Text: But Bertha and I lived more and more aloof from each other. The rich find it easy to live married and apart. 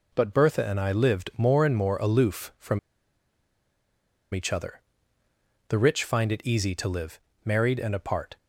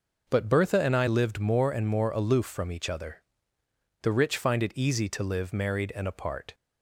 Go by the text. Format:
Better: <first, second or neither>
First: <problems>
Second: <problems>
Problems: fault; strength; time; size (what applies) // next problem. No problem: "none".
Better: second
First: pauses between "from" and "each"; strong; at 2.7 s; 1.5 s long // pauses between "live" and "married"; slight; at 7.1 s; 0.28 s long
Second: none